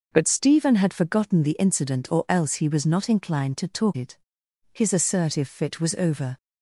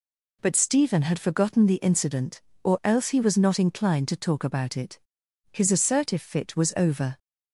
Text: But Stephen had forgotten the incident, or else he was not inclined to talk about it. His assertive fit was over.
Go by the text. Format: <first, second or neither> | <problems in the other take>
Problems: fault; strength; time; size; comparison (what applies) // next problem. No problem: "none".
second | skips "about"; at 3.9 s